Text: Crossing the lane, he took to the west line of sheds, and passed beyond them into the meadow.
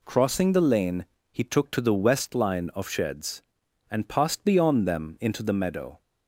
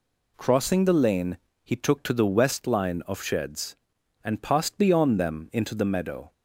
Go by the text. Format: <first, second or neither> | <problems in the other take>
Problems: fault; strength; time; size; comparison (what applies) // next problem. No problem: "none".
neither | none